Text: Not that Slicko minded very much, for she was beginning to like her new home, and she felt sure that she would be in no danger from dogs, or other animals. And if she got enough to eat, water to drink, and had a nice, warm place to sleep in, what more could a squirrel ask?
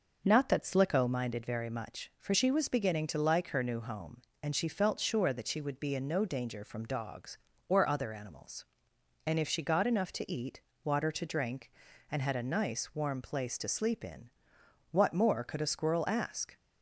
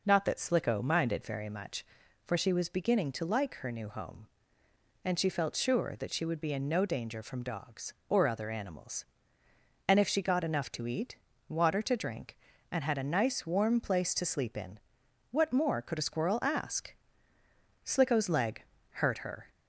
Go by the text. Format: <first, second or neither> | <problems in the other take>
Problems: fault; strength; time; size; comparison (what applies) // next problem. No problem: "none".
first | goes on to say "Slicko's leg hurt her"; strong; from 17.8 s on; 1.6 s long